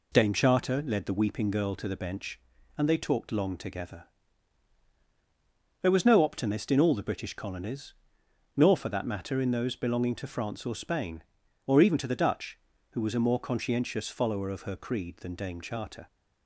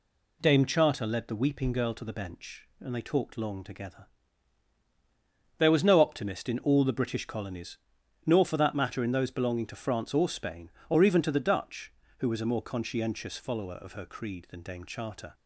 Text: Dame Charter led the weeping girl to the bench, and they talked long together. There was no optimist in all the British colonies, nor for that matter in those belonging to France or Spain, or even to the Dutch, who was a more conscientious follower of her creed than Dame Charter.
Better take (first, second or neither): neither